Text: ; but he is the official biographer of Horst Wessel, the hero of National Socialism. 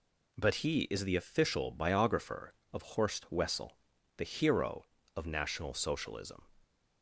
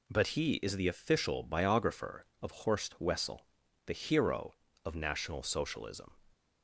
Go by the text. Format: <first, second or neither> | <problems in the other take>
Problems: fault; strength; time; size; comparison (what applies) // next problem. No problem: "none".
neither | none